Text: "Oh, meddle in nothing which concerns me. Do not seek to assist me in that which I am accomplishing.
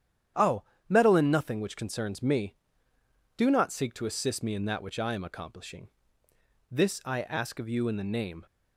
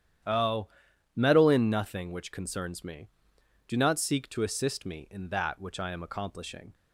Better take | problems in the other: second | starts louder than the rest; strong; until 1.6 s; 9.5 dB; strong in the second // goes on to say "This I ask of you in the name"; strong; from 6.6 s on; 1.7 s long

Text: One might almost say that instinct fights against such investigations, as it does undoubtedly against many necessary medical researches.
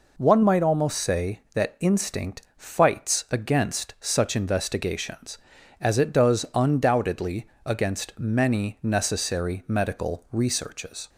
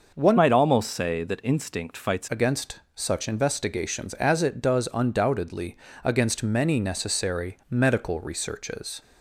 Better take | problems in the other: first | starts louder than the rest; noticeable; until 1.1 s; 6 dB // changes voice from "might" to "fights"; from 0.3 to 2.2 s; 1.9 s long // pauses between "undoubtedly" and "against"; slight; at 5.7 s; 0.26 s long; slight in the first

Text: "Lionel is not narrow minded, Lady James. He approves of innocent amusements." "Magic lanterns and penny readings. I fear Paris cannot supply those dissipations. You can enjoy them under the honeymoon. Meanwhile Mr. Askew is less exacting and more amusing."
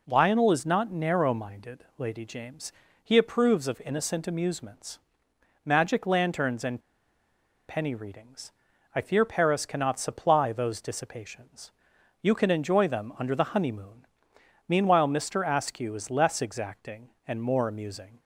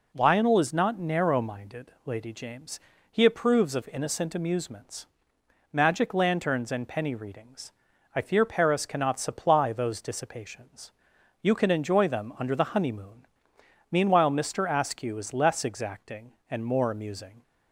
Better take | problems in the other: second | pauses between "and" and "penny"; noticeable; at 6.8 s; 0.88 s long

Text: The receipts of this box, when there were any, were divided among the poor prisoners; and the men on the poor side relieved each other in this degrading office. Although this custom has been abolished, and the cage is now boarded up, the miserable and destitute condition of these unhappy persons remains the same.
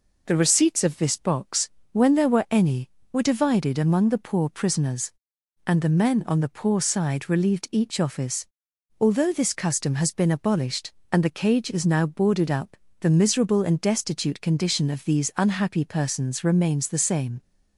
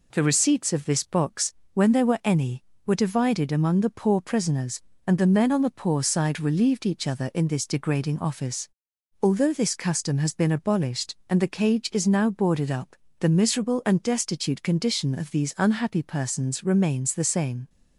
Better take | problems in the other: second | skips "other in this degrading"; at 7.9 s

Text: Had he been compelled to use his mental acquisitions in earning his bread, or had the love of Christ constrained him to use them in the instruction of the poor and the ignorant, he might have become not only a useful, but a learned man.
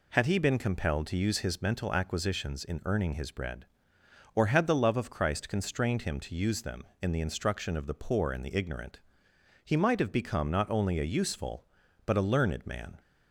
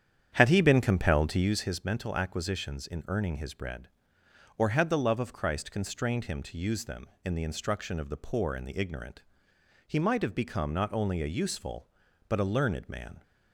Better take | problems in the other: first | starts louder than the rest; strong; until 1.6 s; 9 dB

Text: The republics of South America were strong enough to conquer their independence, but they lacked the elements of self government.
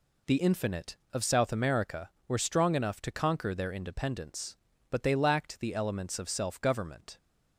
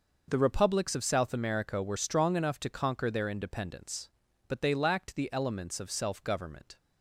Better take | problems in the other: second | says "infinite" for "republics"; at 0.3 s

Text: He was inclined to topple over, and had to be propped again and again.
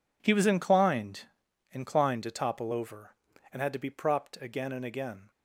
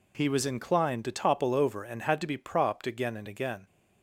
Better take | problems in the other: second | says "inclined" twice; at 1.7 s

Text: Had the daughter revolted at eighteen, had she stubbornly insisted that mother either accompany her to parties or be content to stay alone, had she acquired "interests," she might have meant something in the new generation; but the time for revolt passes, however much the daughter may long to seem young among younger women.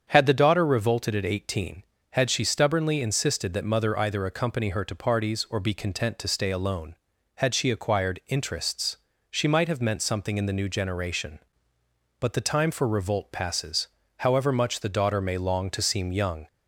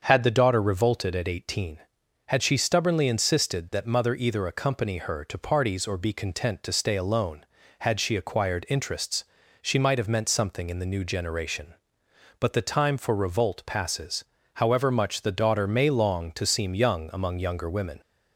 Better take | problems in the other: second | starts louder than the rest; strong; until 1.1 s; 7.5 dB; also in the second // stops before "among younger women"; at 16.4 s

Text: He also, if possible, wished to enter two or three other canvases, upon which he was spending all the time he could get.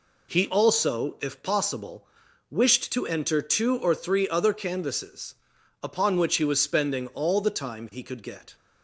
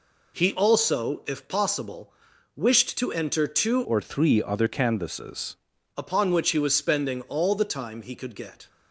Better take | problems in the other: first | changes voice from "or" to "canvases"; from 3.8 to 5.5 s; 1.7 s long

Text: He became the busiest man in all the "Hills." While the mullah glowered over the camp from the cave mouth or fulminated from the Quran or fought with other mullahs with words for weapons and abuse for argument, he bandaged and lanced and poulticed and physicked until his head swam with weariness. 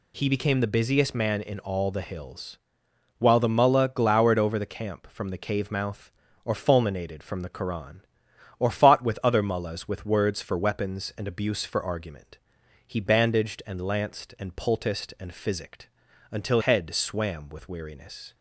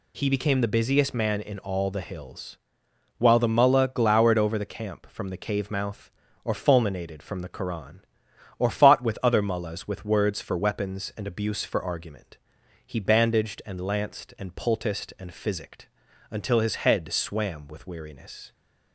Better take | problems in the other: second | pauses between "physicked" and "until"; at 15.8 s; 0.42 s long; also in the second // skips "his"; at 16.6 s

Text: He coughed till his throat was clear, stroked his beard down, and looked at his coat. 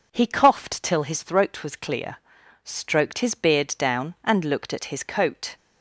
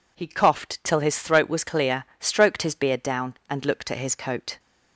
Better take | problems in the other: neither | none

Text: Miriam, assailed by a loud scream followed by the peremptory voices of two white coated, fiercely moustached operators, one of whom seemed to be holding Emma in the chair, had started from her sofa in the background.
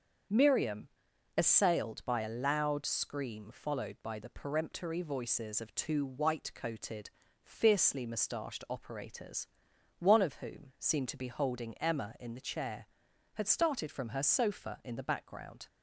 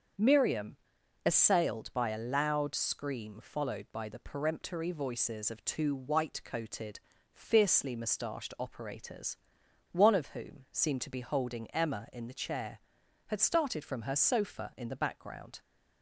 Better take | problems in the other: neither | starts louder than the rest; the same in both

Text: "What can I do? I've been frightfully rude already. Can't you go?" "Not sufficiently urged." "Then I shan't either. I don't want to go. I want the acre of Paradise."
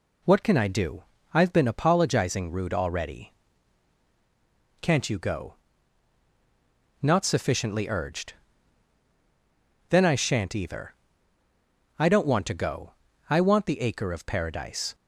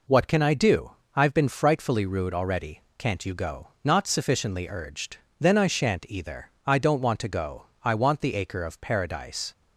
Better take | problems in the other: second | says "apologizing" for "frightfully"; at 1.6 s

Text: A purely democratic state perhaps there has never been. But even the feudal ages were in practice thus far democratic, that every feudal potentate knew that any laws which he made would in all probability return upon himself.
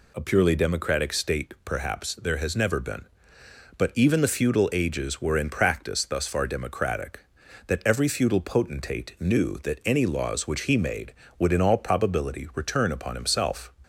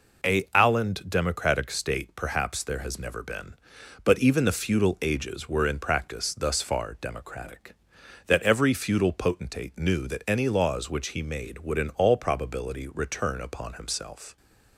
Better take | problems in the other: first | says "alland" for "purely"; at 0.5 s

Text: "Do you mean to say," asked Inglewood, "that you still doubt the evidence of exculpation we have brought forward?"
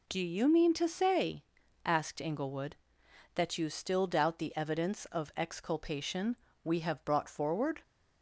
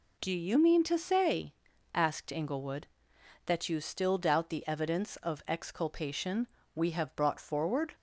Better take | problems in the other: neither | pauses between "exculpation" and "we"; slight; the same in both

